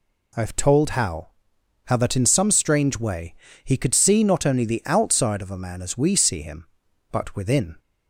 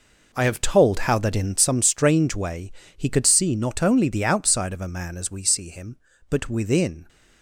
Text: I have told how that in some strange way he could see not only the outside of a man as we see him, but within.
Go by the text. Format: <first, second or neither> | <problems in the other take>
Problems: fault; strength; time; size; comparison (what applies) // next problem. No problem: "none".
second | says "how" twice; at 1.8 s // pauses between "way" and "he"; slight; at 3.3 s; 0.30 s long; slight in the second